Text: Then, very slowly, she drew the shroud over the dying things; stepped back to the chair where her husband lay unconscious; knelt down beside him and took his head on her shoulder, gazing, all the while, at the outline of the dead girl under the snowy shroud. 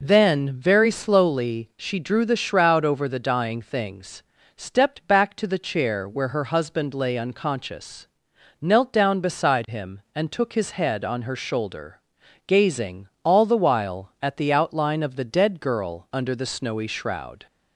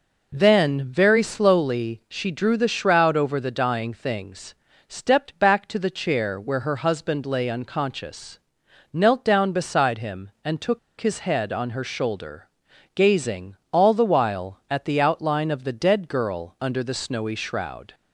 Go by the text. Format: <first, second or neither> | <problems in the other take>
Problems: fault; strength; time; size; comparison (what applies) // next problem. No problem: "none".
first | pauses between "took" and "his"; slight; at 10.7 s; 0.20 s long